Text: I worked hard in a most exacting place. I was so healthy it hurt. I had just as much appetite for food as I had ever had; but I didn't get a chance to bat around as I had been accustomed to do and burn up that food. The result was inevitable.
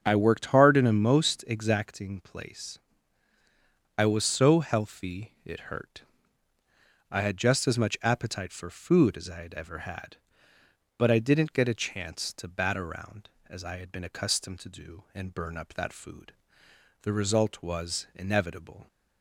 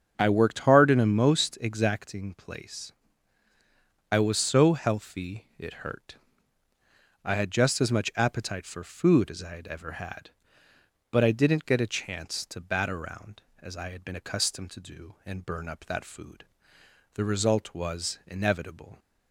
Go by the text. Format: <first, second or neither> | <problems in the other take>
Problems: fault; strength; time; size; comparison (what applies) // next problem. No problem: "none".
neither | starts louder than the rest; the same in both